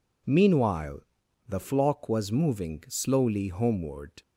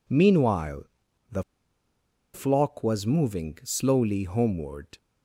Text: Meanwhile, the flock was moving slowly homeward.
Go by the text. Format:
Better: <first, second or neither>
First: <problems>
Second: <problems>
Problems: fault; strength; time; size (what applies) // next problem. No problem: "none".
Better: first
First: none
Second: pauses between "the" and "flock"; noticeable; at 1.4 s; 0.91 s long